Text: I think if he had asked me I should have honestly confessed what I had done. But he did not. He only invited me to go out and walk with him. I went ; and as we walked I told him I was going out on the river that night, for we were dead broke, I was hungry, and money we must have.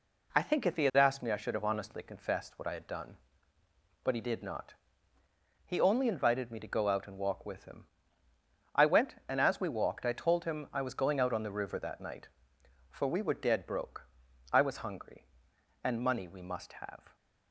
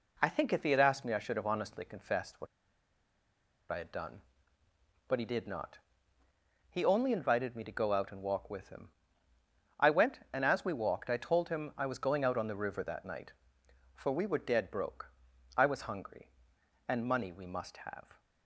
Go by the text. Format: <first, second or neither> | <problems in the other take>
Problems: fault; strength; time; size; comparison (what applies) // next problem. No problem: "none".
first | pauses between "what" and "I"; strong; at 2.4 s; 1.2 s long